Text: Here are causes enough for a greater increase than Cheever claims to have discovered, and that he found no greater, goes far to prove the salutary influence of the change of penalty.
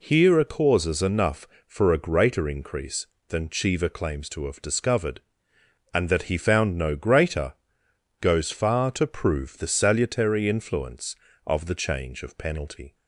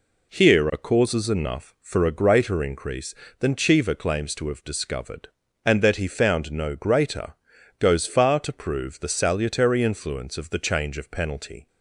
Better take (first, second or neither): neither